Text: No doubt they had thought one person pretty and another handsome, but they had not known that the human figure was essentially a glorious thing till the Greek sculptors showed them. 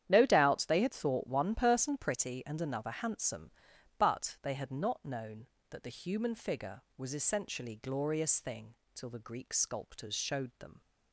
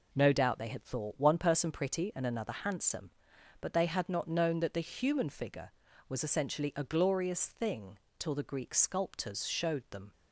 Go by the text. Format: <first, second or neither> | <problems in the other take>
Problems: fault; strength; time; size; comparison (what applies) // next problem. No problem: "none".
second | starts louder than the rest; strong; until 1.0 s; 10 dB // skips "a"; at 7.7 s // pauses between "thing" and "till"; slight; at 8.7 s; 0.18 s long; slight in the second